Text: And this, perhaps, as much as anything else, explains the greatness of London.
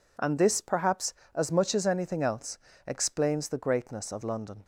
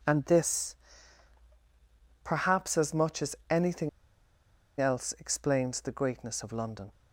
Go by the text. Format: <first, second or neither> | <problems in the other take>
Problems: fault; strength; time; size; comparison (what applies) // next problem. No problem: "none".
first | pauses between "anything" and "else"; noticeable; at 3.8 s; 0.91 s long